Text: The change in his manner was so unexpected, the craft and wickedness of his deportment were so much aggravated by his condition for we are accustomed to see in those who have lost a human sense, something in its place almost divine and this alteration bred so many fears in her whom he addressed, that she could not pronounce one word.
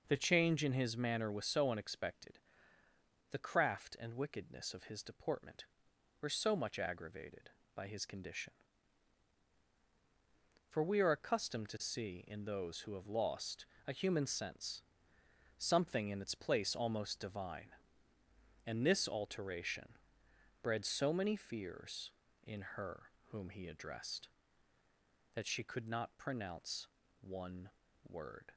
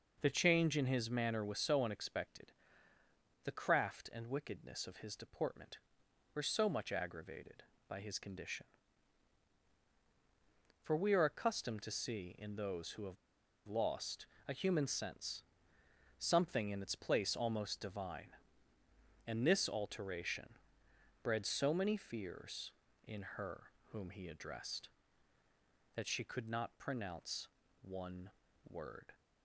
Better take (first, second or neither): first